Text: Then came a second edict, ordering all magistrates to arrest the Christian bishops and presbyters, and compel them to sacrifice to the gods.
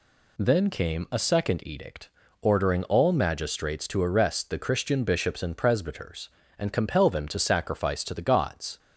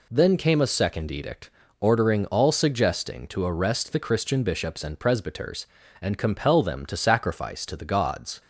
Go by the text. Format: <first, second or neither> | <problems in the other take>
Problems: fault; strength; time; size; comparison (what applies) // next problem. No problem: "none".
first | says "suggesting" for "magistrates"; at 2.4 s